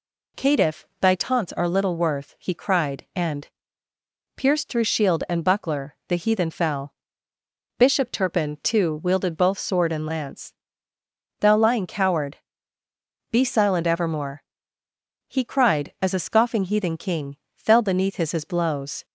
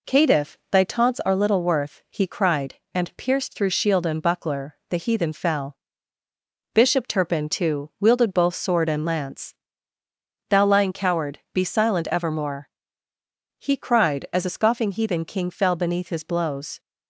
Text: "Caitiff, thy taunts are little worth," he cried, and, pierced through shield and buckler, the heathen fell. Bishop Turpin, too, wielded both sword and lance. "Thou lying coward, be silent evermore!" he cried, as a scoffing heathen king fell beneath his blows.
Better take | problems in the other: second | pauses between "king" and "fell"; slight; at 17.3 s; 0.18 s long // says "his" twice; at 18.3 s

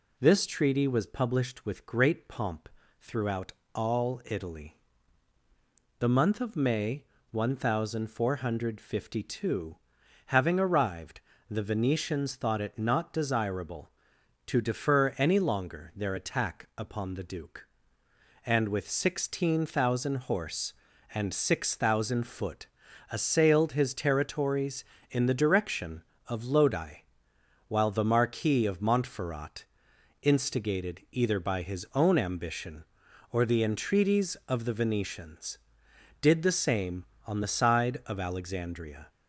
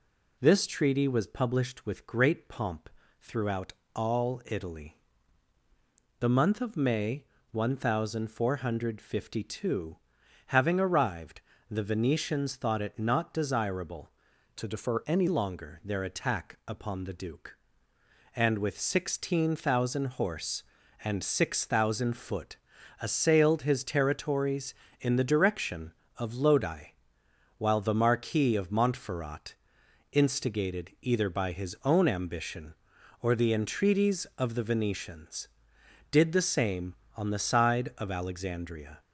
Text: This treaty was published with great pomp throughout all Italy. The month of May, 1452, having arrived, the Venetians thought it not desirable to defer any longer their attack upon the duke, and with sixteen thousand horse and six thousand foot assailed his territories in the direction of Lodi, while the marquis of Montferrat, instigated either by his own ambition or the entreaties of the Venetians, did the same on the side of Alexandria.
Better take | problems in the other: first | pauses between "pomp" and "throughout"; slight; at 2.8 s; 0.30 s long; slight in the first // pauses between "throughout" and "all"; slight; at 3.7 s; 0.24 s long; slight in the first // changes voice from "to" to "any"; from 14.5 to 15.2 s; 0.7 s long // pauses between "foot" and "assailed"; at 22.5 s; 0.44 s long; also in the first

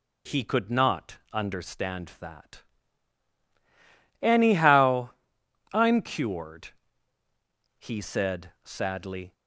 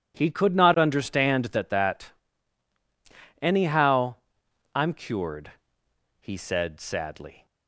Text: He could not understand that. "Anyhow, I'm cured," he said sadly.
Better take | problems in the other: first | says "that" twice; at 1.6 s

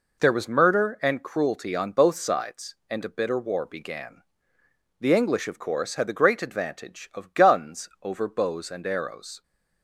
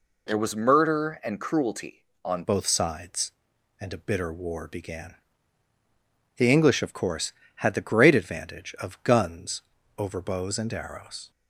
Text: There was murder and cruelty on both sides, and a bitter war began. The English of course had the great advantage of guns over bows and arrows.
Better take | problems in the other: first | changes voice at "both"; from 2.4 s on; 8.9 s long // pauses between "guns" and "over"; slight; at 9.6 s; 0.36 s long

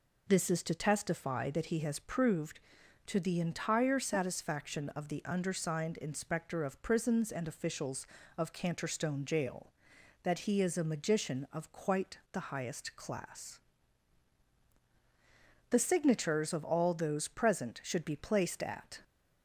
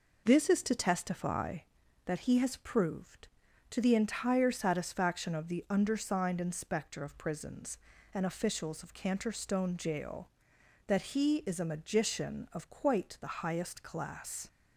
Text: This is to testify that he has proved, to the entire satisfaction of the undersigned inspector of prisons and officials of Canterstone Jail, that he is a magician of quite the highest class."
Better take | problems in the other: second | pauses between "quite" and "the"; slight; at 12.1 s; 0.16 s long // goes on to say "The signatures of all those present should be placed at"; strong; from 15.6 s on; 3.3 s long

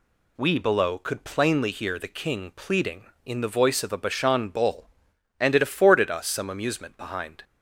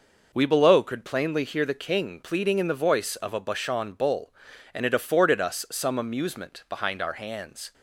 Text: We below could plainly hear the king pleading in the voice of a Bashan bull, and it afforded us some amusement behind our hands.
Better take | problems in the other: second | stops before "our hands"; at 7.4 s

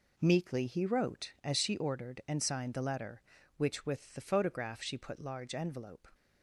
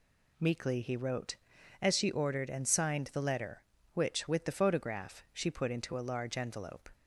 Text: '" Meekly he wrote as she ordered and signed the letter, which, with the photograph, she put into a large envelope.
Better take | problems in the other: second | skips "into a"; at 5.1 s

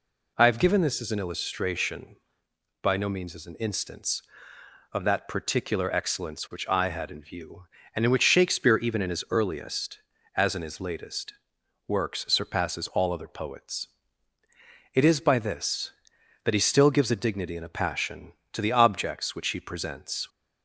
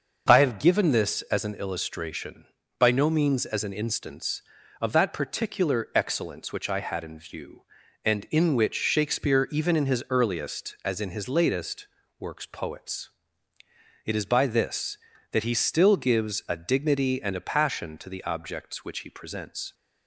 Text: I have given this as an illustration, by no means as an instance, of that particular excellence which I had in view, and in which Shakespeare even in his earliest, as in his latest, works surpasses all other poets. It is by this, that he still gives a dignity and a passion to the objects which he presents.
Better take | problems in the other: first | skips "surpasses all other"; at 12.4 s

